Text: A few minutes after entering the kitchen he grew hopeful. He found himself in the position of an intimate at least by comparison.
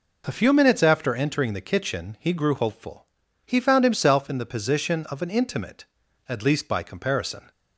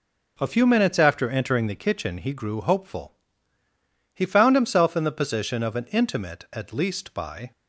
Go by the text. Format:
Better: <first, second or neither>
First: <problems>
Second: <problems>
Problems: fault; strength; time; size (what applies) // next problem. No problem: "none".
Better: first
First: none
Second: stops before "comparison"; at 7.5 s